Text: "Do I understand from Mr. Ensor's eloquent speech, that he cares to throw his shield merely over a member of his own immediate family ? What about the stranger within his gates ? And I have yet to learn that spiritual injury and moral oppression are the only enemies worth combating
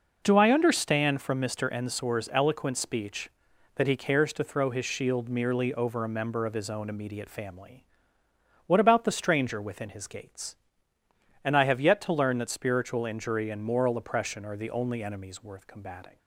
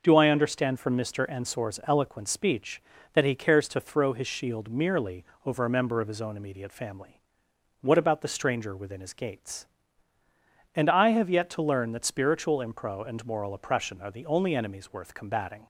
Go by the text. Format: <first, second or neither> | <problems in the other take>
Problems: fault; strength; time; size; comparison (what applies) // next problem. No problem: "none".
first | pauses between "merely" and "over"; slight; at 5.2 s; 0.20 s long // says "impro" for "injury"; at 12.5 s